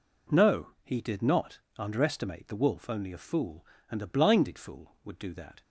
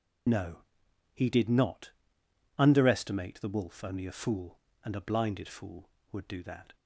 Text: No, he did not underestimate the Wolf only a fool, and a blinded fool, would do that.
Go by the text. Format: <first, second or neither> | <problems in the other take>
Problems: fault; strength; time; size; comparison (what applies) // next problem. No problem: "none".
first | loses the start of "No"; at 0.2 s; 40 ms // pauses between "not" and "underestimate"; noticeable; at 1.9 s; 0.68 s long; slight in the first